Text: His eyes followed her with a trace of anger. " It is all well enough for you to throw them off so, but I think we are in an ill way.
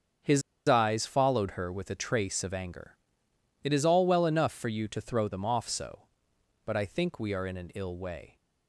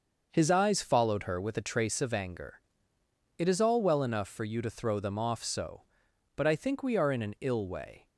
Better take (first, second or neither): second